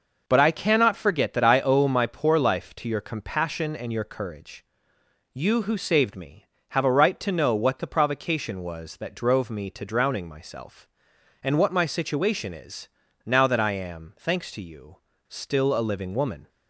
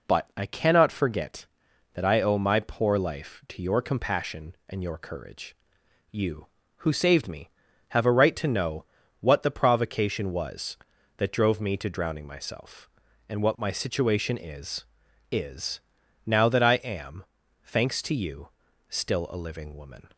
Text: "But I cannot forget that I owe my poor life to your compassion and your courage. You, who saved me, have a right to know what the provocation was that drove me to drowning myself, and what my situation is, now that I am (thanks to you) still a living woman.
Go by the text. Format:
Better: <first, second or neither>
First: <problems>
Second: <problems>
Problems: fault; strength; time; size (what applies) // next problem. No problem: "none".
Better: first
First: none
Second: pauses between "know" and "what"; slight; at 8.8 s; 0.34 s long // says "is" twice; at 15.3 s